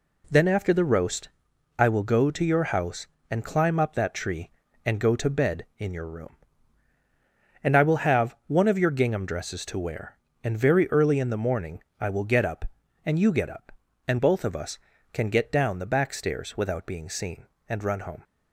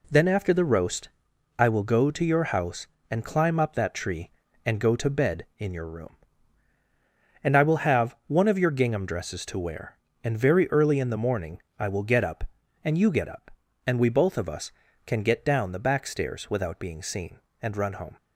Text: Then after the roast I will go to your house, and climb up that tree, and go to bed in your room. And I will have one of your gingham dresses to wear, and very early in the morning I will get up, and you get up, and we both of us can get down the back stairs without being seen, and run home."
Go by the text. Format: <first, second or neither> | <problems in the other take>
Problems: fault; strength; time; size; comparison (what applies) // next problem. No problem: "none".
second | pauses between "roast" and "I"; noticeable; at 1.2 s; 0.48 s long; noticeable in the second // pauses between "morning" and "I"; slight; at 11.8 s; 0.18 s long; slight in the second // skips "we"; at 14.1 s